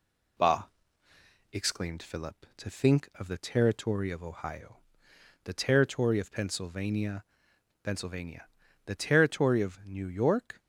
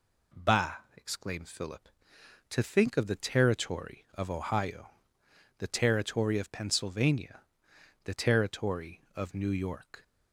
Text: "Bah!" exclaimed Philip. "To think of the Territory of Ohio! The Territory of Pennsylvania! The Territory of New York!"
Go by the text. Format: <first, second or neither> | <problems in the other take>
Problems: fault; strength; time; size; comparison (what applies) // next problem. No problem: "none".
second | says "Pennsylvania" twice; at 7.8 s